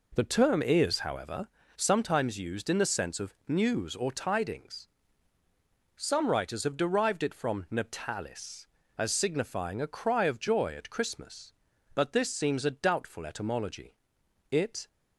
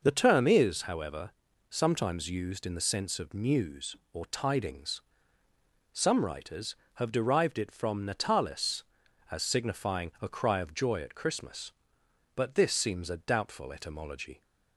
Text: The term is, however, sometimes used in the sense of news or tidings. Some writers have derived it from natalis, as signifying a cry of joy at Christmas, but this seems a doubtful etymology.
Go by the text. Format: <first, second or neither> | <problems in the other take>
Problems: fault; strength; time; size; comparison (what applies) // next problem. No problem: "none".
second | goes on to say "It"; slight; from 14.5 s on; 0.36 s long